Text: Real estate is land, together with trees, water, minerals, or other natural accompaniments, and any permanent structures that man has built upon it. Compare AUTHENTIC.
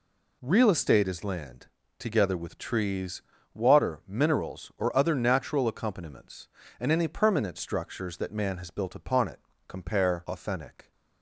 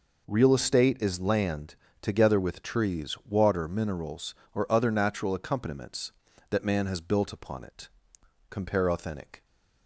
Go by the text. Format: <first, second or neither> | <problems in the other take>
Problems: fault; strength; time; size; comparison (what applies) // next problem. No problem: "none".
first | skips "and any permanent structures"; at 6.3 s